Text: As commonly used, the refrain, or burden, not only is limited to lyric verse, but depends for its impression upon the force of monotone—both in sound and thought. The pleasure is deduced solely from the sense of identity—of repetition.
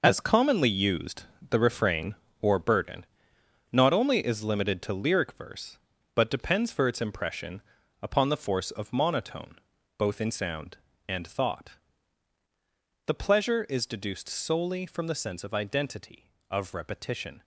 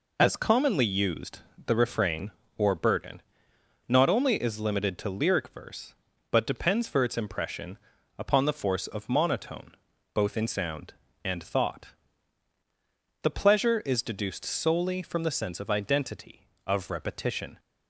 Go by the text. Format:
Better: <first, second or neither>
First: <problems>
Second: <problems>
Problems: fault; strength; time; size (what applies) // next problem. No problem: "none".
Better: second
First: gets quieter; strong; throughout; 10 dB // pauses between "impression" and "upon"; at 7.6 s; 0.42 s long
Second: pauses between "impression" and "upon"; at 7.7 s; 0.42 s long